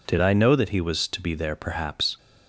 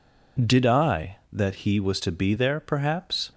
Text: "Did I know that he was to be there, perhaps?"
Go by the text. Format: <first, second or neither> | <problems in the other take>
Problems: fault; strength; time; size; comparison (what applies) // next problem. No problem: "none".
first | skips "know"; at 1.2 s